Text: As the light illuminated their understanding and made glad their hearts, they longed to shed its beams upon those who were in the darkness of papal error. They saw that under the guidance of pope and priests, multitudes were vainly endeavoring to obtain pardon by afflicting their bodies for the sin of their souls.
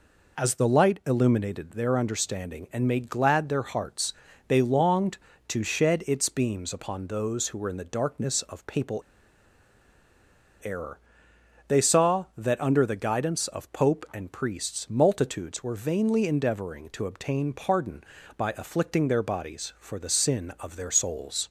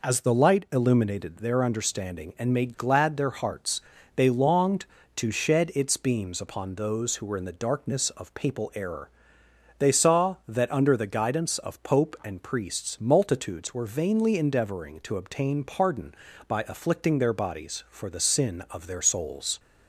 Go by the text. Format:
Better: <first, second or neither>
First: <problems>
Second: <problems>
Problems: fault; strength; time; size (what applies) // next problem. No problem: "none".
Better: second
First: pauses between "papal" and "error"; strong; at 9.0 s; 1.6 s long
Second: none